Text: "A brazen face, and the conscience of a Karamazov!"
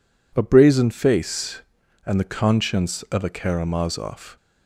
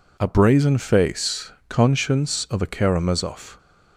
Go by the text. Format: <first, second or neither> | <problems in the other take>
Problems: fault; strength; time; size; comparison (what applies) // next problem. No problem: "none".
first | skips "and the"; at 1.5 s